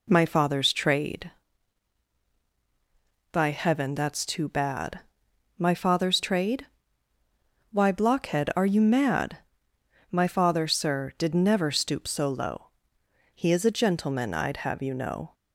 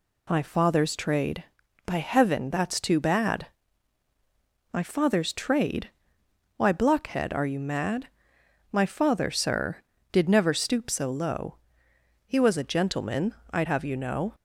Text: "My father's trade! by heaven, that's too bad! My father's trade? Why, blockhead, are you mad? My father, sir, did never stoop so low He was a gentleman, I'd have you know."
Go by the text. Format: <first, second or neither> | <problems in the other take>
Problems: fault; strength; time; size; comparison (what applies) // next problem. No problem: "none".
second | pauses between "low" and "He"; noticeable; at 12.6 s; 0.68 s long; noticeable in the second // says "is" for "was"; at 13.5 s